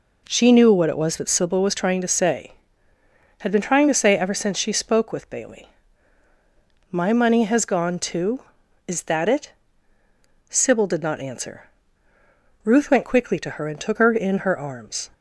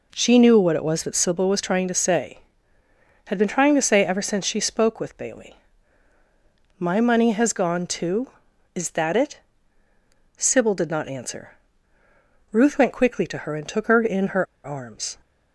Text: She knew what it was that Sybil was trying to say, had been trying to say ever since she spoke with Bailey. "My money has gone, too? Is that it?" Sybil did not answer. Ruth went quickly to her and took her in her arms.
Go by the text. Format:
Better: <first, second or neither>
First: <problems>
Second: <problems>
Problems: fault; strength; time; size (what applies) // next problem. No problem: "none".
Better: first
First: none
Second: pauses between "her" and "arms"; slight; at 14.4 s; 0.20 s long